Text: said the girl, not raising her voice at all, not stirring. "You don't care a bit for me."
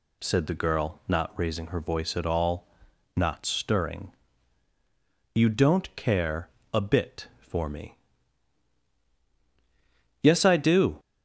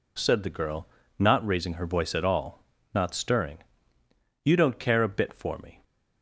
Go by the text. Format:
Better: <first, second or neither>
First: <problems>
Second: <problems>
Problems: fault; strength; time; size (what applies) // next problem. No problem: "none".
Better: second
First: pauses between "care" and "a"; slight; at 6.4 s; 0.24 s long // goes on to say "Yes I do"; noticeable; from 10.2 s on; 0.78 s long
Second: none